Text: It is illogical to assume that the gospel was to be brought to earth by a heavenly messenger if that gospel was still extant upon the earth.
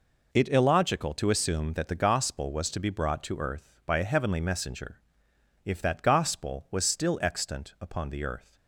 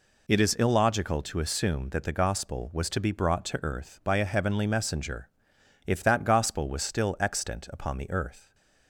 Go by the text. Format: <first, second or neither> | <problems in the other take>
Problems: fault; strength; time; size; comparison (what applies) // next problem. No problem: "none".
second | skips "is"; at 0.4 s // pauses between "messenger" and "if"; noticeable; at 5.0 s; 0.64 s long; noticeable in the second